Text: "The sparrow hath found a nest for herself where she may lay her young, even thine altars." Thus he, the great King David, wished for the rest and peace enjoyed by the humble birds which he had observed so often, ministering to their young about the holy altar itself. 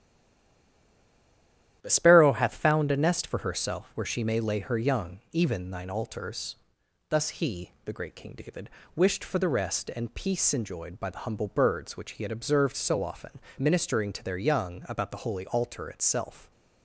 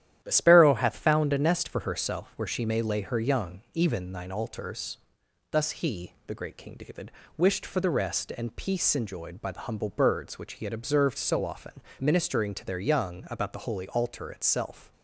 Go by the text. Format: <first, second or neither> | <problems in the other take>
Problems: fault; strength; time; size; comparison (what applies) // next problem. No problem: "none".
second | stays silent before the first word; noticeable; until 1.8 s; 1.8 s long // starts louder than the rest; strong; until 2.8 s; 11 dB; strong in the second